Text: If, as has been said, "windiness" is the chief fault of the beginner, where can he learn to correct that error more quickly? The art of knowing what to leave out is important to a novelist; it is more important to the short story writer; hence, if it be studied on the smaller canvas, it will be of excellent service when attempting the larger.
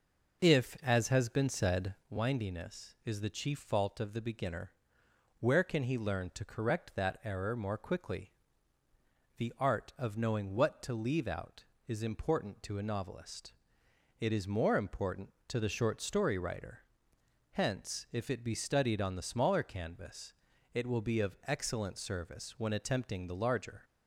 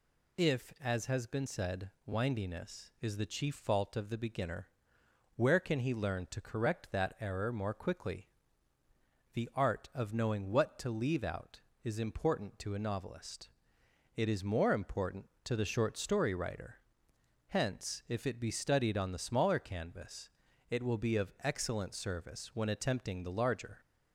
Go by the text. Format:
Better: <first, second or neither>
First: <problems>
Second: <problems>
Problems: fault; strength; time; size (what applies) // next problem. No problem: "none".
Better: second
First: starts louder than the rest; noticeable; until 2.1 s; 5 dB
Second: none